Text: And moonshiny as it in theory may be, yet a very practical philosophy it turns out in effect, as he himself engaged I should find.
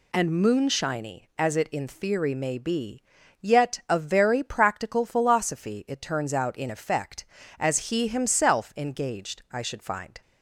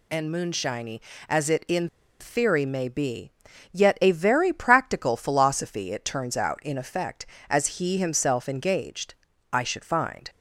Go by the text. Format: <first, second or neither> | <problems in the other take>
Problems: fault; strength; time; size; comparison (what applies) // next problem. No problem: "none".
first | pauses between "in" and "theory"; slight; at 1.8 s; 0.33 s long // pauses between "engaged" and "I"; slight; at 9.1 s; 0.36 s long